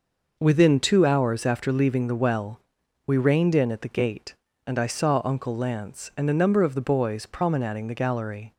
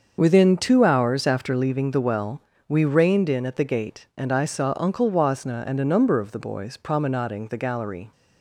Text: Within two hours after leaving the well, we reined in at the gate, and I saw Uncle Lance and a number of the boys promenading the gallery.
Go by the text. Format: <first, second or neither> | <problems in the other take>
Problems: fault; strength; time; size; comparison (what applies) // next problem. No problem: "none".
first | starts louder than the rest; until 1.2 s; 6.5 dB // says "Wasna" for "Lance"; at 5.0 s